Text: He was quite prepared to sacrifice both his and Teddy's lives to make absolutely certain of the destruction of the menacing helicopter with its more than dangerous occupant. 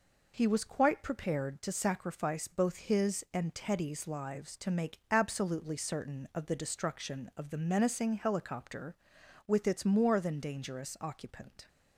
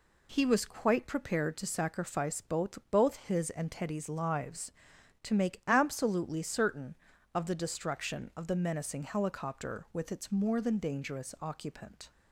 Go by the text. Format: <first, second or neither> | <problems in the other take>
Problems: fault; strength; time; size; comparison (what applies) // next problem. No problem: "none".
first | says "both" twice; at 2.9 s